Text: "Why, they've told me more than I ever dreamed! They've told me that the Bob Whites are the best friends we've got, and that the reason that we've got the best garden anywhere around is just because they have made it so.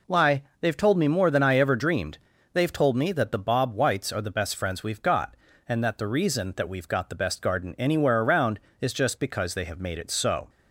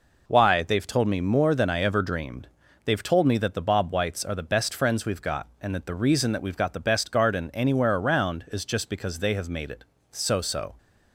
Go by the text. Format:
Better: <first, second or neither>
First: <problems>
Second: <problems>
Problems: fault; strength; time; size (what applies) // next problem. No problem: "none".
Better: first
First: none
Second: says "so" twice; at 10.4 s